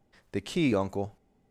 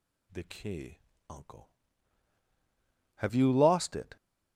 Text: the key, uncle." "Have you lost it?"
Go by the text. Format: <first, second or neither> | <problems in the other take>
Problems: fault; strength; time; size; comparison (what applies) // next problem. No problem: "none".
second | stops before "Have you lost it"; at 1.1 s